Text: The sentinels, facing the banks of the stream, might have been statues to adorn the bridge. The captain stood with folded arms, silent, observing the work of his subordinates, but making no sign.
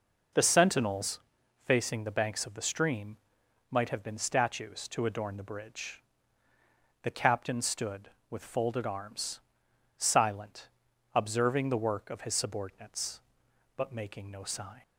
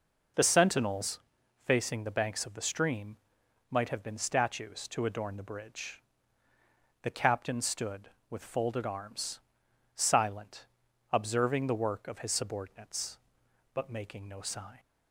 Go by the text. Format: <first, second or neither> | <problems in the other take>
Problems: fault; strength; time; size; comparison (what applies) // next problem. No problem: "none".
neither | none